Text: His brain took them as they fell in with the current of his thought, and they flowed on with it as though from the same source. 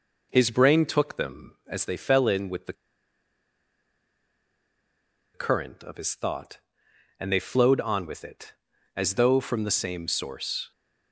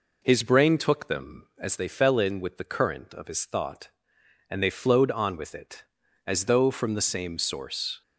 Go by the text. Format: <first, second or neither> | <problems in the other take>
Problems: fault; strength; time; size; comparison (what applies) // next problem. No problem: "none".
second | pauses between "the" and "current"; strong; at 2.7 s; 2.6 s long